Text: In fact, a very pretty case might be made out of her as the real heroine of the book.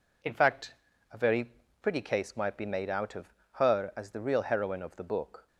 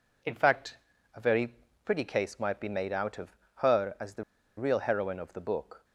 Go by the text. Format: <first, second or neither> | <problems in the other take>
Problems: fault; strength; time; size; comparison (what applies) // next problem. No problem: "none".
first | pauses between "very" and "pretty"; slight; at 1.5 s; 0.32 s long; slight in the first // pauses between "of" and "her"; slight; at 3.3 s; 0.20 s long; slight in the first // pauses between "the" and "real"; slight; at 4.2 s; 0.34 s long